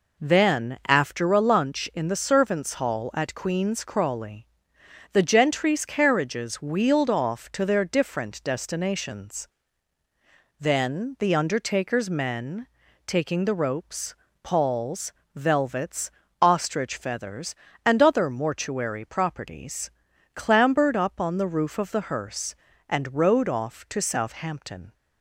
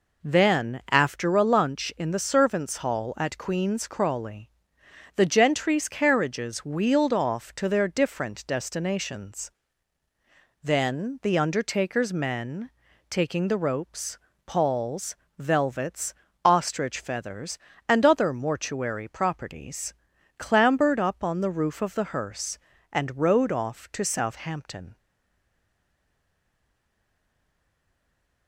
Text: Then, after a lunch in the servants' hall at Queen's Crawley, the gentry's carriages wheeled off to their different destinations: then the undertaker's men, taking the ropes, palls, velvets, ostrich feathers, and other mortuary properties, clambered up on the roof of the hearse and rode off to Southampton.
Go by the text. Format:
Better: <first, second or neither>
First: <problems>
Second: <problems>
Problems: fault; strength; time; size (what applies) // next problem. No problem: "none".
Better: first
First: none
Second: stays silent after the last word; strong; from 24.9 s on; 3.5 s long